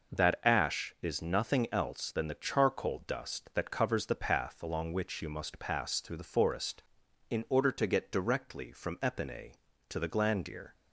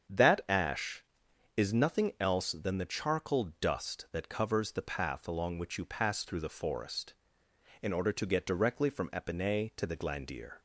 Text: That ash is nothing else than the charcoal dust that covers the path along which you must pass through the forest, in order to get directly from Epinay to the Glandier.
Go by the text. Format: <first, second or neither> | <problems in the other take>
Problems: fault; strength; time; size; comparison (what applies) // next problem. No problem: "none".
first | starts louder than the rest; strong; until 1.7 s; 7.5 dB // skips "must"; at 5.8 s